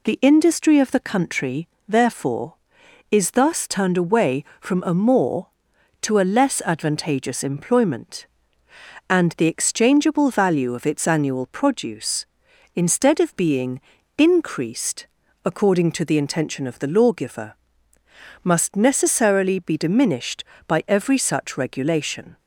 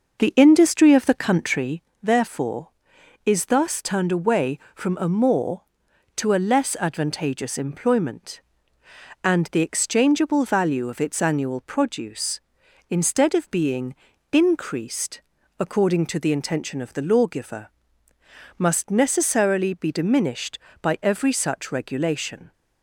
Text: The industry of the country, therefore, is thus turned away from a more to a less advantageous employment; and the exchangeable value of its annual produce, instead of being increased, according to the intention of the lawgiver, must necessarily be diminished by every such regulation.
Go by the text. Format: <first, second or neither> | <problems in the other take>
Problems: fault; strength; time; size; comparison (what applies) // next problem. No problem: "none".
first | starts louder than the rest; noticeable; until 1.8 s; 6 dB // pauses between "being" and "increased"; slight; at 13.9 s; 0.36 s long; slight in the first